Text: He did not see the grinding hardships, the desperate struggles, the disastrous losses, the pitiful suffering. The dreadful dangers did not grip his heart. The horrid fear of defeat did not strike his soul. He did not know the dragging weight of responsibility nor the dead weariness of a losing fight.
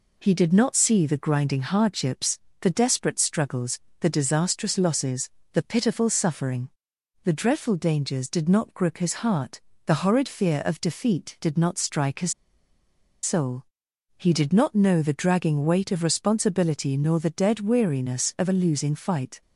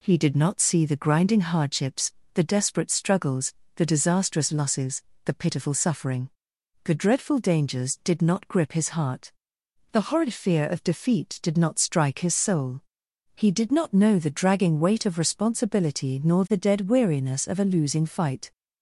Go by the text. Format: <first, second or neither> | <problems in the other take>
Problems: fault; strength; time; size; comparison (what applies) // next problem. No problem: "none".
second | pauses between "his" and "soul"; noticeable; at 12.3 s; 0.90 s long